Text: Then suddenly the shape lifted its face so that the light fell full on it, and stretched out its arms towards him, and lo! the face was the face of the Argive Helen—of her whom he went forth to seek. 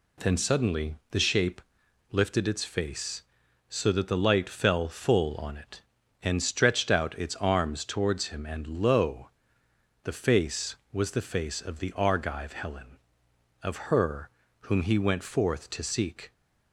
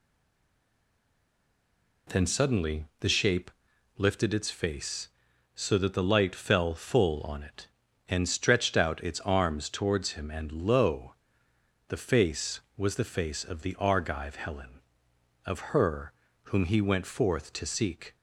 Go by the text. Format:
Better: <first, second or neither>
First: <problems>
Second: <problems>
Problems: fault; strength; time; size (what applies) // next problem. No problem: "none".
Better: first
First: pauses between "shape" and "lifted"; noticeable; at 1.6 s; 0.51 s long // pauses between "her" and "whom"; slight; at 14.3 s; 0.30 s long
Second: stays silent before the first word; noticeable; until 2.0 s; 2.0 s long // pauses between "shape" and "lifted"; noticeable; at 3.5 s; 0.48 s long // pauses between "her" and "whom"; slight; at 16.1 s; 0.30 s long